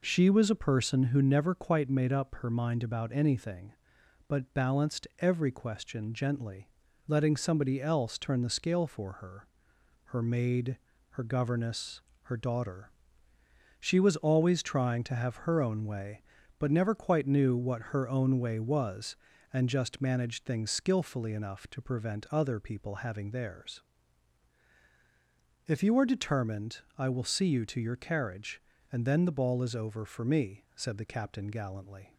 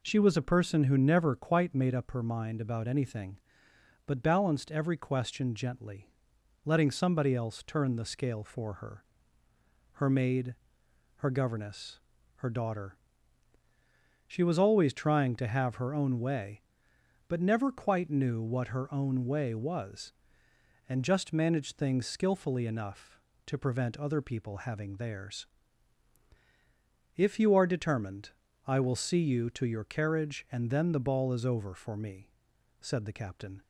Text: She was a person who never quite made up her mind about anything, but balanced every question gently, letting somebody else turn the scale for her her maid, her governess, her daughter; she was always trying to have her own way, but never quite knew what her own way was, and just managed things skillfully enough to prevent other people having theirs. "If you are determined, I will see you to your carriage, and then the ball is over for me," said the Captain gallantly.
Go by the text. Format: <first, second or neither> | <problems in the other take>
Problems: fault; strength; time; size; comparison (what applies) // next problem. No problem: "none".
first | pauses between "her" and "her"; noticeable; at 9.0 s; 0.92 s long; noticeable in the first // stops before "gallantly"; at 33.6 s